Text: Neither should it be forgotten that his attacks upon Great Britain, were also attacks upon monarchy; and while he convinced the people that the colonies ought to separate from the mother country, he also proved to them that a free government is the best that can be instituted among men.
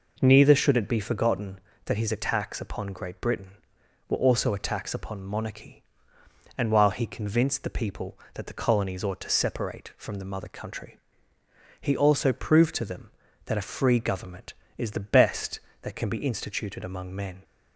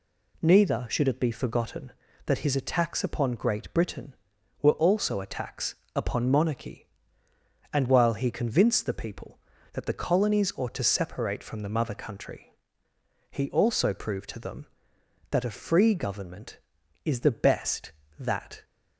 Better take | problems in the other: first | pauses between "attacks" and "upon"; slight; at 5.7 s; 0.18 s long // stops before "can be instituted among men"; at 18.6 s

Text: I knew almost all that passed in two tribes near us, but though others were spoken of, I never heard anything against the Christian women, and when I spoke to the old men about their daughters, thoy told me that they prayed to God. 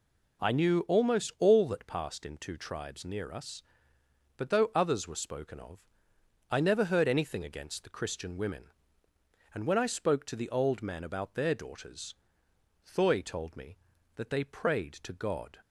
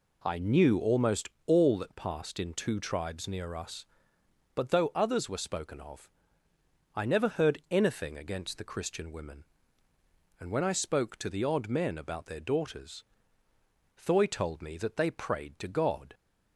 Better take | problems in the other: first | pauses between "almost" and "all"; slight; at 1.2 s; 0.18 s long // says "odd" for "old"; at 11.4 s

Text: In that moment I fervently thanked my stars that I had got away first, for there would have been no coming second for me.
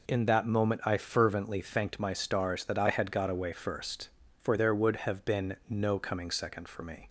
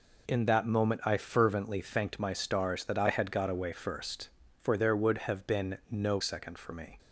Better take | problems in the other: first | skips "coming"; at 6.1 s

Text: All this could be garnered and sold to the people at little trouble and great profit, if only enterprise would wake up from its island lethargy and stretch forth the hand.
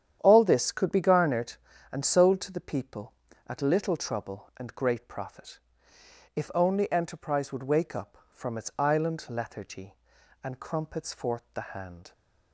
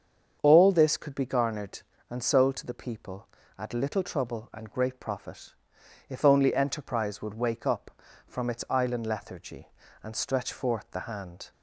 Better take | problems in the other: second | starts louder than the rest; strong; until 1.2 s; 9.5 dB; strong in the second // says "crumpets" for "stretch"; at 10.6 s

